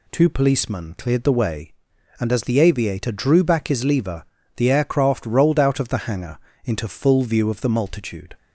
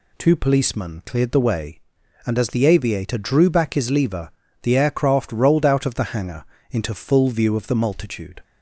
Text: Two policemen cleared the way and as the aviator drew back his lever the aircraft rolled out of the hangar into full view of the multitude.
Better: neither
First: pauses between "lever" and "the"; slight; at 4.2 s; 0.32 s long // pauses between "hangar" and "into"; slight; at 6.3 s; 0.26 s long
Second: pauses between "lever" and "the"; slight; at 4.3 s; 0.32 s long // pauses between "hangar" and "into"; slight; at 6.4 s; 0.26 s long

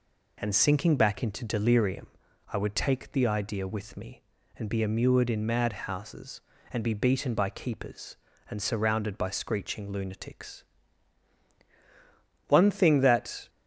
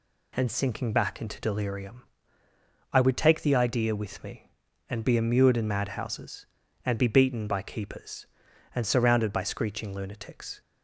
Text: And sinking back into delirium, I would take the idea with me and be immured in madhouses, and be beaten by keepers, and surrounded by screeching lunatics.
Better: second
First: goes on to say "One thing that"; noticeable; from 12.4 s on; 1.0 s long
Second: none

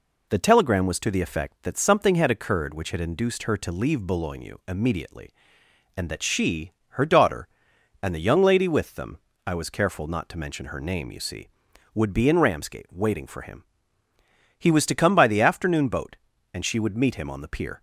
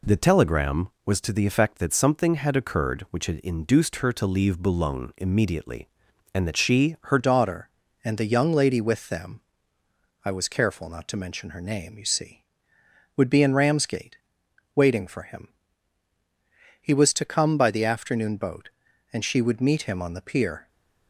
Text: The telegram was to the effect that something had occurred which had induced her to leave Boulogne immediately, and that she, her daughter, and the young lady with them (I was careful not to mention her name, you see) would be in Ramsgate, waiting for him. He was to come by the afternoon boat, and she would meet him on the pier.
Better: first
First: none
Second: changes voice at "daughter"; from 7.1 s on; 13.5 s long

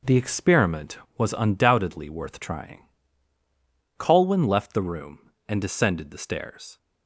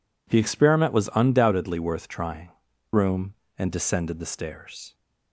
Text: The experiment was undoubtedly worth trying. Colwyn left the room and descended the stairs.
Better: first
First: none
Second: skips "Colwyn left the"; at 2.7 s

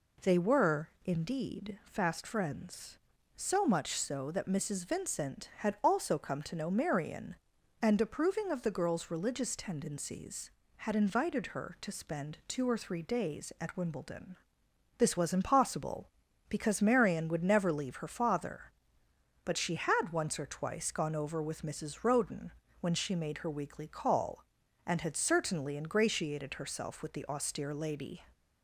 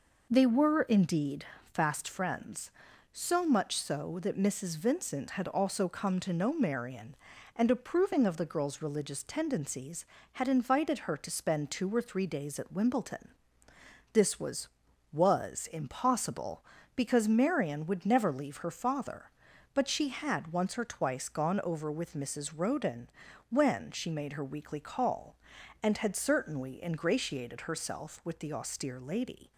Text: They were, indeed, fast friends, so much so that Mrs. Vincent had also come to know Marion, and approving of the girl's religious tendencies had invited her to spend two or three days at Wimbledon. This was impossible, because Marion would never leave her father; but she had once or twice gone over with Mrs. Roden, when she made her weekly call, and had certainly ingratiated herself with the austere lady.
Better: first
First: none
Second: says "was" twice; at 15.1 s

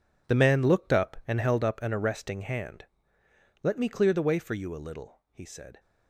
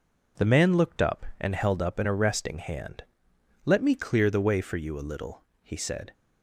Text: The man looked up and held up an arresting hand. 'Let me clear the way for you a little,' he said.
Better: second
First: gets quieter; strong; throughout; 13.5 dB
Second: none

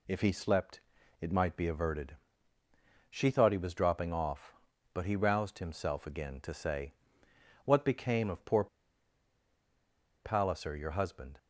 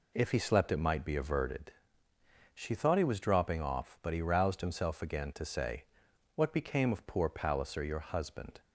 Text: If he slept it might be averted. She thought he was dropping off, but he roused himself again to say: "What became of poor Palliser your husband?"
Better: second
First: pauses between "slept" and "it"; at 0.8 s; 0.40 s long // pauses between "poor" and "Palliser"; strong; at 8.6 s; 1.5 s long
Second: none

